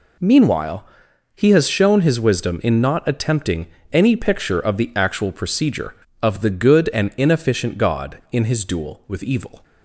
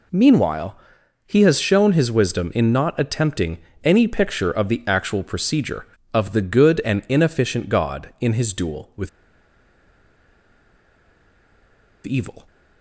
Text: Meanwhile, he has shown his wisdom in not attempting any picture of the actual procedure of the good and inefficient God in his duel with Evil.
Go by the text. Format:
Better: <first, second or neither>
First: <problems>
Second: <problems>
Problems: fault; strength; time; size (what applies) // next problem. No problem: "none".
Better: first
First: pauses between "attempting" and "any"; slight; at 3.6 s; 0.24 s long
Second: pauses between "attempting" and "any"; slight; at 3.5 s; 0.24 s long // pauses between "with" and "Evil"; strong; at 9.0 s; 2.9 s long